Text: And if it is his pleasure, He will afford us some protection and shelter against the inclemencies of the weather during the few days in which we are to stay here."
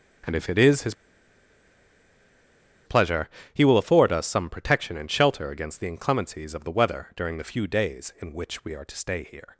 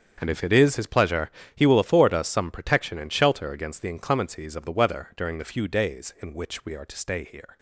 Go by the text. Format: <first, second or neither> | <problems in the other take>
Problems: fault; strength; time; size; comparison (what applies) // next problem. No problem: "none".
second | starts louder than the rest; strong; until 3.1 s; 7 dB; strong in the second // pauses between "his" and "pleasure"; strong; at 0.9 s; 1.9 s long